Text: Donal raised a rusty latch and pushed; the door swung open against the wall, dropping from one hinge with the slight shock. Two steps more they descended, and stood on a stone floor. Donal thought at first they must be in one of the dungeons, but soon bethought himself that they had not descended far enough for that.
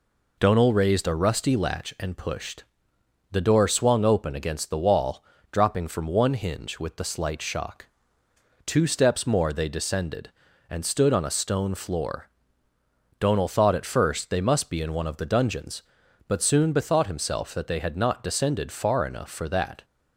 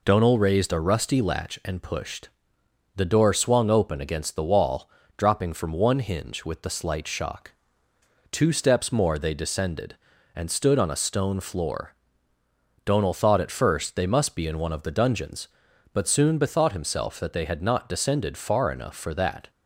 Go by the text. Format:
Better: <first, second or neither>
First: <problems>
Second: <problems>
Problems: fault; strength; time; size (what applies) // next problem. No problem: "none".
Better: neither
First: none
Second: none